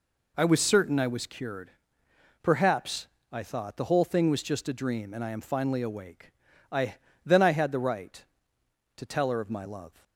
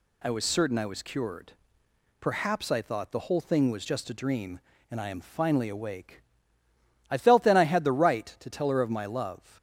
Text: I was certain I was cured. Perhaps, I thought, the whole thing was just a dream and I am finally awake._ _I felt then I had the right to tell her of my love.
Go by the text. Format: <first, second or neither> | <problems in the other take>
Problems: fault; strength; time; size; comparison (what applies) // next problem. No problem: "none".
second | skips "felt"; at 7.0 s